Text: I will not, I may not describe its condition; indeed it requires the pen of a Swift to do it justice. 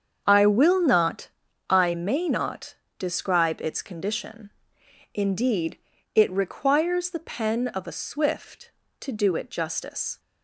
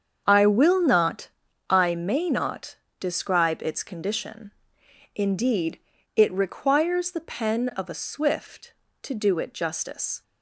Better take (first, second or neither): neither